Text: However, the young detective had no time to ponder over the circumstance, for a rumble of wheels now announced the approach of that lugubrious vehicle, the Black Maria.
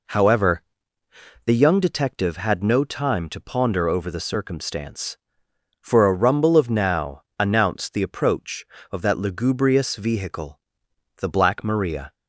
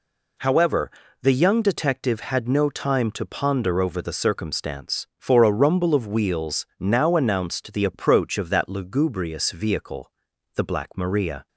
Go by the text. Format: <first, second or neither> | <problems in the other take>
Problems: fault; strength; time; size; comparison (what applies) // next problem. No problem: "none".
second | skips "wheels"; at 6.6 s // pauses between "now" and "announced"; slight; at 7.2 s; 0.16 s long